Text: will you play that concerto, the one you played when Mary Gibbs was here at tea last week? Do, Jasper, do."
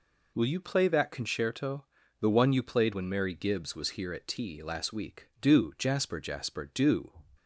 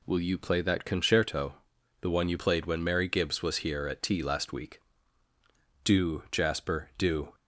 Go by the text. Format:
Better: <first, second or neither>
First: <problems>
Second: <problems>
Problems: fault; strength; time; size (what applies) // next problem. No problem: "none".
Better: second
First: says "Jasper" twice; at 6.1 s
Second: none